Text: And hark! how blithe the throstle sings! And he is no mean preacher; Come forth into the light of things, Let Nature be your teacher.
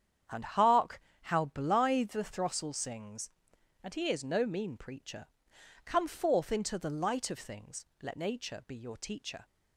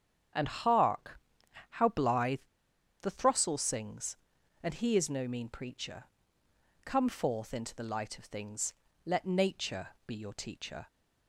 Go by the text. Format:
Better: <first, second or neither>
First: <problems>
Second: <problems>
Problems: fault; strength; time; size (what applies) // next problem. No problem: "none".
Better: first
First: starts louder than the rest; strong; until 1.5 s; 8.5 dB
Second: starts louder than the rest; strong; until 1.8 s; 7.5 dB // pauses between "blithe" and "the"; noticeable; at 2.3 s; 0.61 s long // pauses between "Nature" and "be"; slight; at 9.8 s; 0.18 s long